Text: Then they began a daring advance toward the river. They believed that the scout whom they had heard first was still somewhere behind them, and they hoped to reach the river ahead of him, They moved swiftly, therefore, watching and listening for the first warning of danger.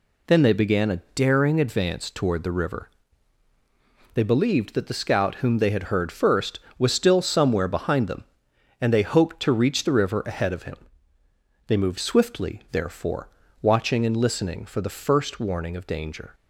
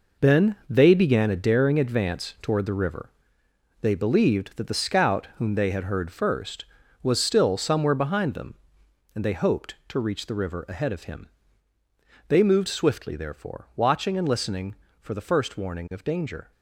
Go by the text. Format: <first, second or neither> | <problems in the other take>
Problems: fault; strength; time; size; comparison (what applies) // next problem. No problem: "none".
first | gets quieter; strong; throughout; 9 dB